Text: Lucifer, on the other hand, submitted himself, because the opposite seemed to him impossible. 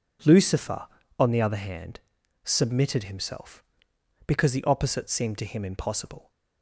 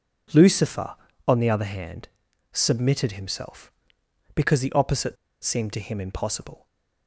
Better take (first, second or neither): first